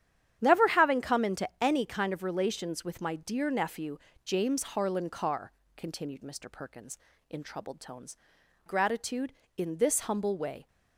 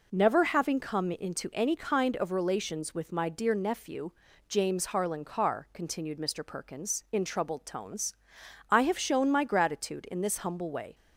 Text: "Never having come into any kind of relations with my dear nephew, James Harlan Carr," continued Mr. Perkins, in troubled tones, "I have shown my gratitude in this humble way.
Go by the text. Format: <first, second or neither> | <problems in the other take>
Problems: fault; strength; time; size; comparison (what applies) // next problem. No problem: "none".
second | starts louder than the rest; strong; until 1.4 s; 10 dB // skips "I have shown my"; at 8.4 s